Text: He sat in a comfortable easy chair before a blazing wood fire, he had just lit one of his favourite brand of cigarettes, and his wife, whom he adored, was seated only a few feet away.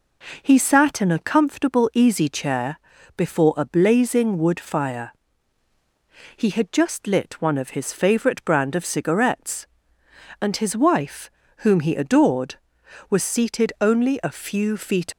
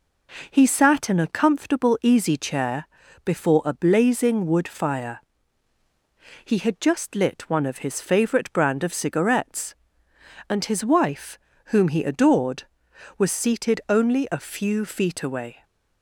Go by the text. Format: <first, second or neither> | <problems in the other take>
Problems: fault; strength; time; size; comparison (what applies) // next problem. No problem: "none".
second | pauses between "chair" and "before"; at 2.7 s; 0.38 s long; also in the second // stops before "away"; at 15.1 s